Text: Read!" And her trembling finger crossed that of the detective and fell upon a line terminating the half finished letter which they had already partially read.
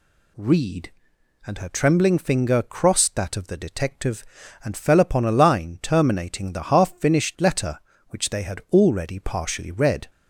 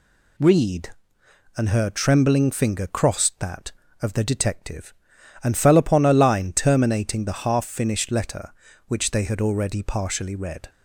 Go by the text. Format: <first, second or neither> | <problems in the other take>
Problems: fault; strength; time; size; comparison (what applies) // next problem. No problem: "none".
neither | none